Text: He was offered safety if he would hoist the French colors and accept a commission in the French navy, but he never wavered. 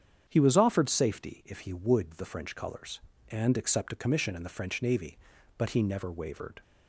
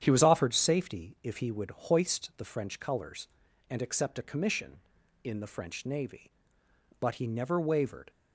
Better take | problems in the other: second | starts louder than the rest; strong; until 1.3 s; 8 dB; strong in the second // skips "hoist"; at 2.1 s

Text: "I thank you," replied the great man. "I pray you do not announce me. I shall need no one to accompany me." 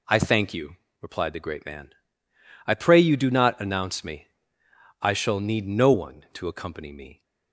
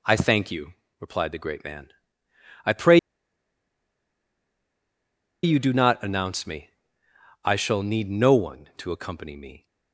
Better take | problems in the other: first | pauses between "pray" and "you"; strong; at 2.9 s; 2.4 s long

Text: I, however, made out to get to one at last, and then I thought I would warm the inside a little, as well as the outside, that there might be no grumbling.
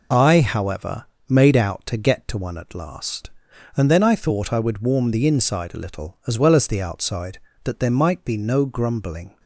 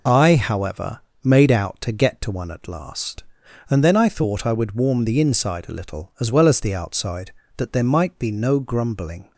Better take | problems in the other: neither | none

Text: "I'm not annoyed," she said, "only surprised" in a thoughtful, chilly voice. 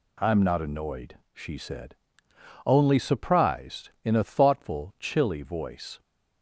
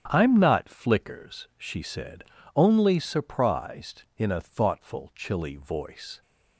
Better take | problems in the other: first | starts louder than the rest; strong; until 1.1 s; 9 dB // says "flickers" for "annoyed"; at 0.6 s

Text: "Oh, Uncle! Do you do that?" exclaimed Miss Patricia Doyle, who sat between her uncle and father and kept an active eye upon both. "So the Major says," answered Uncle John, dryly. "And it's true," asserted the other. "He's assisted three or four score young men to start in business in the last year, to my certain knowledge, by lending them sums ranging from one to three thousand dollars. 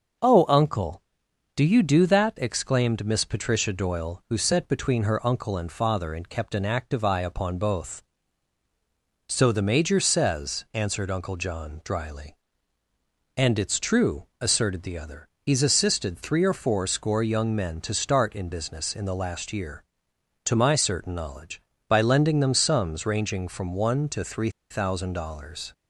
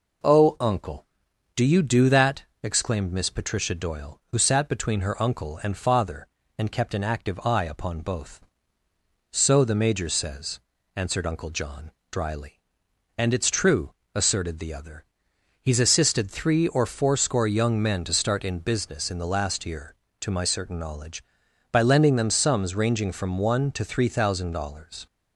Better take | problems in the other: second | starts louder than the rest; noticeable; until 1.8 s; 6 dB // pauses between "three" and "thousand"; slight; at 24.4 s; 0.20 s long

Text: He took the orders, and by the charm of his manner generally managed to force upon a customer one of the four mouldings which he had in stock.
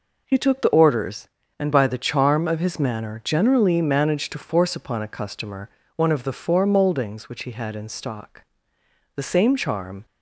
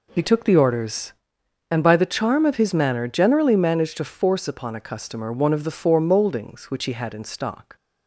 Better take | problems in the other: second | pauses between "customer" and "one"; slight; at 5.6 s; 0.28 s long // goes on to say "The same charm"; noticeable; from 9.1 s on; 0.90 s long

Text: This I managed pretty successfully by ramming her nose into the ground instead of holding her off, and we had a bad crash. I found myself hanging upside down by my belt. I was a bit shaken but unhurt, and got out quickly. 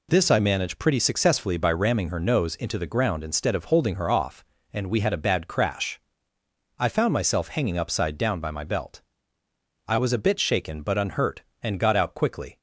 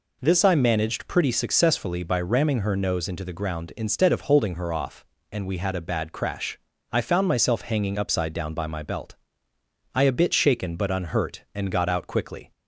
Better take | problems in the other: first | skips "was"; at 10.0 s

